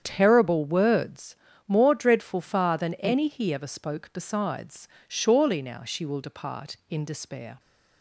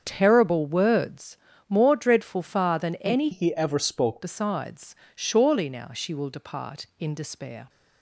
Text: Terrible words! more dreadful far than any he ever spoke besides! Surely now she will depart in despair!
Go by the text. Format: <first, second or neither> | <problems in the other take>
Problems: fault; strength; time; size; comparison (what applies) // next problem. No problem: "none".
first | starts louder than the rest; strong; until 1.0 s; 7.5 dB; strong in the first // changes voice from "he" to "spoke"; from 3.3 to 4.2 s; 0.9 s long